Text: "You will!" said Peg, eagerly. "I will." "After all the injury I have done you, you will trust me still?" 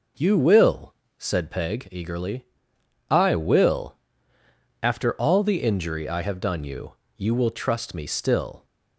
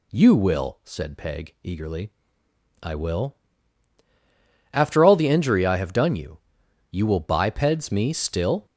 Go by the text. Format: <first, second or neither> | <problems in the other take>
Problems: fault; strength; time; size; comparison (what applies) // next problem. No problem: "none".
first | says "bipeds" for "trust"; at 7.1 s